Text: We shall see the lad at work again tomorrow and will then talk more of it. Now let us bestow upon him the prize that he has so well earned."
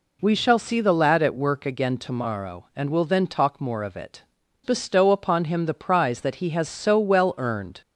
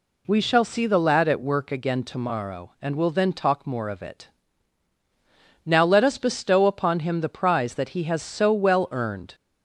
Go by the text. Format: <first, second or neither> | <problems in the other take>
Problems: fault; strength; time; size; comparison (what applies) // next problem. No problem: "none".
second | skips "Now let us"; at 4.4 s